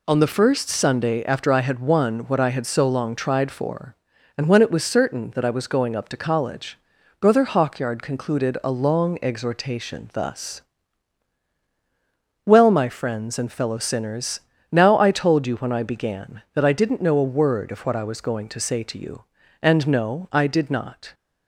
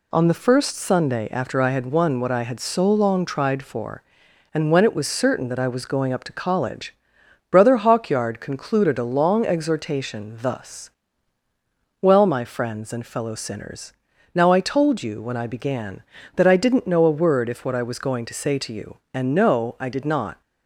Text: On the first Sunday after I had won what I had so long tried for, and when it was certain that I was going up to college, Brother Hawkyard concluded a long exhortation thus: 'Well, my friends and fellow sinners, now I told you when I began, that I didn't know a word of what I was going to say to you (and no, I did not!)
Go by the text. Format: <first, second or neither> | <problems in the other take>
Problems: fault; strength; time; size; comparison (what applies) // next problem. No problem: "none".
first | says "if" for "of"; at 17.4 s